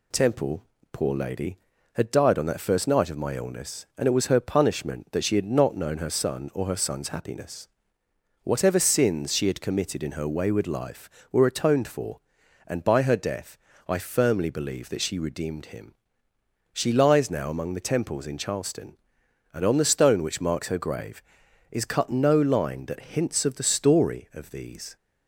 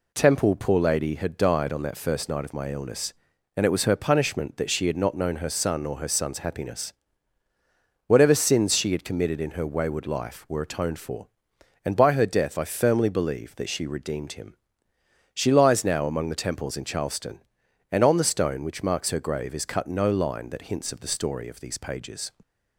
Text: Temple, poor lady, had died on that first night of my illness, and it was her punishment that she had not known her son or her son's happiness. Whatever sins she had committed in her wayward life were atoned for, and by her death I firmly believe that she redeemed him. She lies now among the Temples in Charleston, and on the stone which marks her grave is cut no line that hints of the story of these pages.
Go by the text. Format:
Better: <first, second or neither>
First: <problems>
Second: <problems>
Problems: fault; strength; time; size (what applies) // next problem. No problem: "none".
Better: second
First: pauses between "death" and "I"; slight; at 13.5 s; 0.30 s long // stops before "pages"; at 24.9 s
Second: none